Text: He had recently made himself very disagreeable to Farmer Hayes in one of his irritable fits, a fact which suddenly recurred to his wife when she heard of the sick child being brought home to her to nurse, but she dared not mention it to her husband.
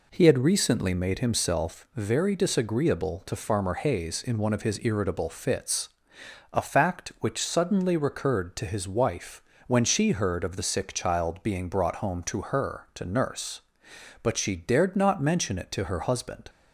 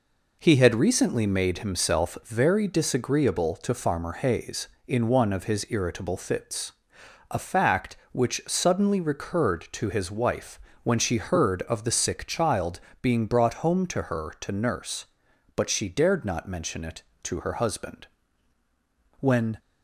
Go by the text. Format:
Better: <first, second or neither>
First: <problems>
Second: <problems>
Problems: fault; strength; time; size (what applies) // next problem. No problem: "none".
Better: first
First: pauses between "wife" and "when"; slight; at 9.4 s; 0.24 s long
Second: pauses between "wife" and "when"; slight; at 10.6 s; 0.24 s long // pauses between "child" and "being"; slight; at 12.7 s; 0.24 s long // goes on to say "When"; slight; from 19.1 s on; 0.40 s long